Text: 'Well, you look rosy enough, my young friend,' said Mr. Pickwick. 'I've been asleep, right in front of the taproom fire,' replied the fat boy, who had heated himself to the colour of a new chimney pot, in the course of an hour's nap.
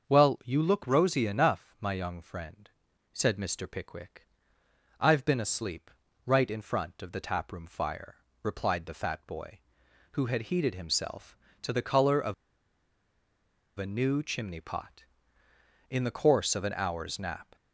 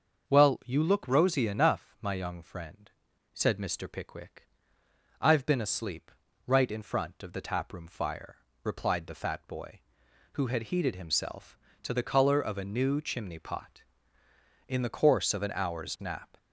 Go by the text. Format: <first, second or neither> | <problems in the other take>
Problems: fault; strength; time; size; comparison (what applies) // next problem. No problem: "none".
second | starts louder than the rest; until 1.1 s; 6.5 dB; also in the second // pauses between "of" and "a"; strong; at 12.3 s; 1.4 s long